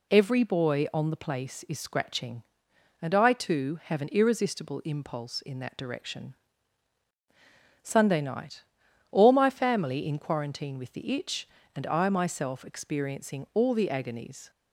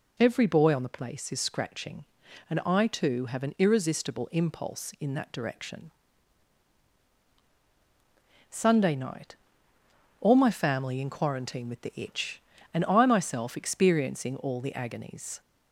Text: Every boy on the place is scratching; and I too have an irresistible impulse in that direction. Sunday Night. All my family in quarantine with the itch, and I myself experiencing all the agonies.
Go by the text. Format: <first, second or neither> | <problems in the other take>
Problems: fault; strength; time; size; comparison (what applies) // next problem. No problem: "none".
neither | none